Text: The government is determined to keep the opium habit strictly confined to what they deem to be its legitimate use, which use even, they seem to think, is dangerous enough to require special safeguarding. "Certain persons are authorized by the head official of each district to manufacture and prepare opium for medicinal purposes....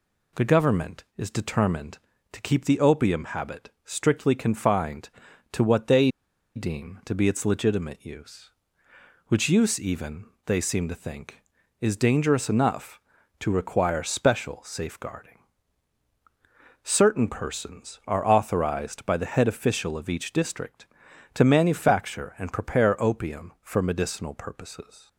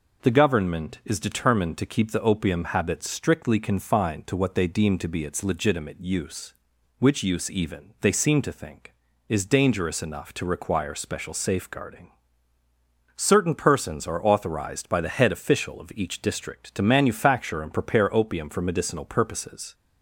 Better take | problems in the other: second | pauses between "habit" and "strictly"; slight; at 3.6 s; 0.16 s long // pauses between "they" and "deem"; noticeable; at 6.0 s; 0.46 s long

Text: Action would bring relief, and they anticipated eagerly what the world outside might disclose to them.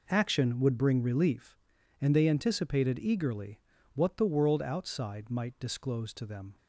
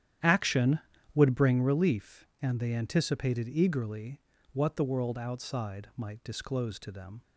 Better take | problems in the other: first | starts louder than the rest; strong; until 1.5 s; 10.5 dB // pauses between "eagerly" and "what"; slight; at 4.1 s; 0.32 s long; slight in the first

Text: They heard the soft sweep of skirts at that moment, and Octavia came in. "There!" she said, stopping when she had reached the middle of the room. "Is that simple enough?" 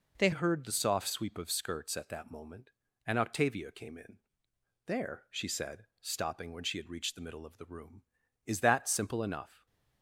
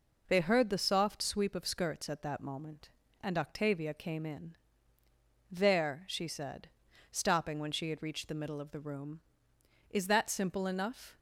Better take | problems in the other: second | changes voice at "heard"; from 0.3 s on; 9.3 s long

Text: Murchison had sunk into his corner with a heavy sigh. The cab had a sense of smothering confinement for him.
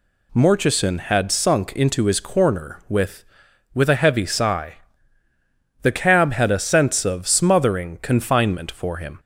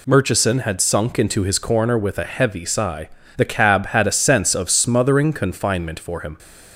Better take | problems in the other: second | says "with" twice; at 3.7 s

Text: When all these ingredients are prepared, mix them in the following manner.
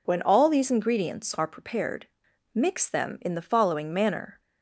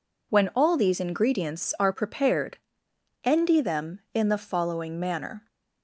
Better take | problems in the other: first | says "endy" for "mix"; at 3.2 s

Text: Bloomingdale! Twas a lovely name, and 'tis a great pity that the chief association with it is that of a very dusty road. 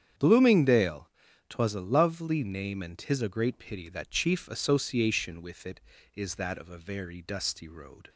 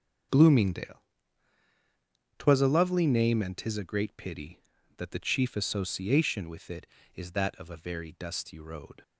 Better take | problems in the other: second | starts louder than the rest; strong; until 1.5 s; 8.5 dB; also in the second // skips "the"; at 4.0 s

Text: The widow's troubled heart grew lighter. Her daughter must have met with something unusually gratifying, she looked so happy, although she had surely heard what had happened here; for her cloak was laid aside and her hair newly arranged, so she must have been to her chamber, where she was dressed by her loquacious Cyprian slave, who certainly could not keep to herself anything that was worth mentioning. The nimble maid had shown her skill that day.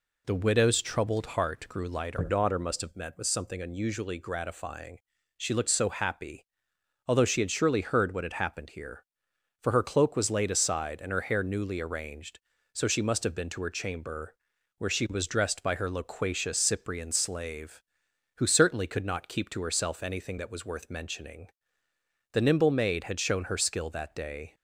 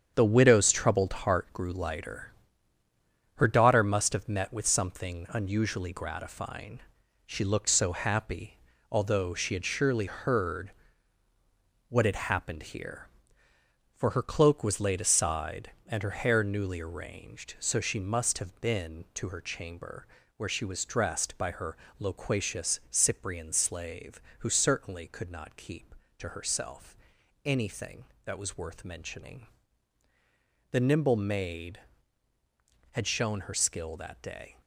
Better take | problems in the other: first | gets quieter; strong; throughout; 8 dB // pauses between "heard" and "what"; at 10.7 s; 1.1 s long // pauses between "her" and "loquacious"; slight; at 21.7 s; 0.22 s long // pauses between "herself" and "anything"; noticeable; at 26.9 s; 0.48 s long

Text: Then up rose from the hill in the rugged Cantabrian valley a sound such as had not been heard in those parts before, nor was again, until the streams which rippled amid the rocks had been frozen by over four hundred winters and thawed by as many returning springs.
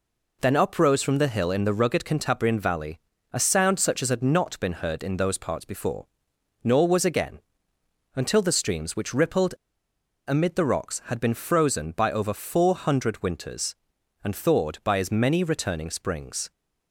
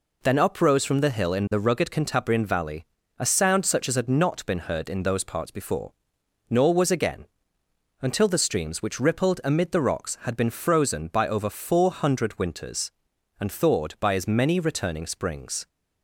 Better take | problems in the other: second | pauses between "valley" and "a"; slight; at 2.9 s; 0.34 s long; slight in the second // pauses between "rippled" and "amid"; noticeable; at 9.5 s; 0.76 s long

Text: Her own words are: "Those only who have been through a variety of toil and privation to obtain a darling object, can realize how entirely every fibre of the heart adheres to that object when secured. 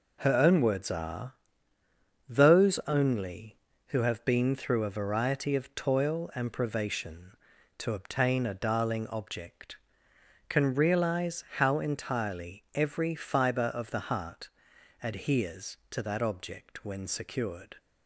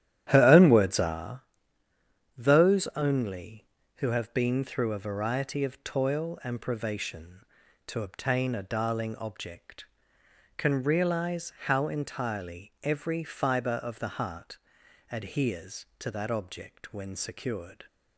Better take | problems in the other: first | starts louder than the rest; strong; until 1.2 s; 11.5 dB // pauses between "heart" and "adheres"; noticeable; at 14.5 s; 0.52 s long; noticeable in the first

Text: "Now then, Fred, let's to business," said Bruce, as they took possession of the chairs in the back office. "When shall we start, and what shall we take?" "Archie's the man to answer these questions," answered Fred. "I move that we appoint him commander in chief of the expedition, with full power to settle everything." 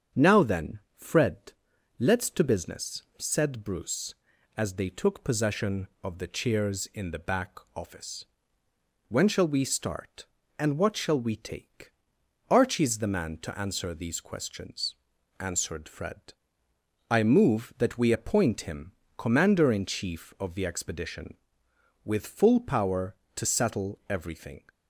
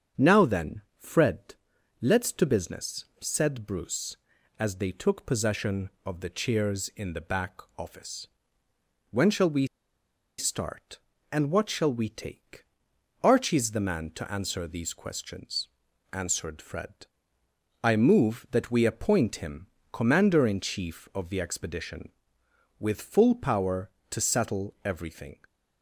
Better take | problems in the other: first | starts louder than the rest; strong; until 1.3 s; 7 dB; strong in the first // pauses between "back" and "office"; slight; at 7.5 s; 0.18 s long; slight in the first // pauses between "we" and "start"; noticeable; at 9.6 s; 0.71 s long // pauses between "him" and "commander"; slight; at 19.6 s; 0.26 s long; slight in the first

